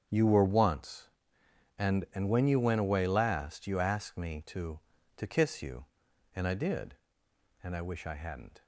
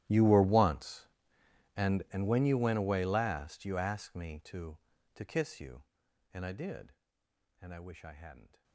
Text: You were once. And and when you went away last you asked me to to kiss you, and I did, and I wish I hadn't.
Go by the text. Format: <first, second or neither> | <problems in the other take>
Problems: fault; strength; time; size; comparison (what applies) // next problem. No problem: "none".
first | gets quieter; strong; throughout; 25 dB // starts louder than the rest; strong; until 1.7 s; 14.5 dB; strong in the first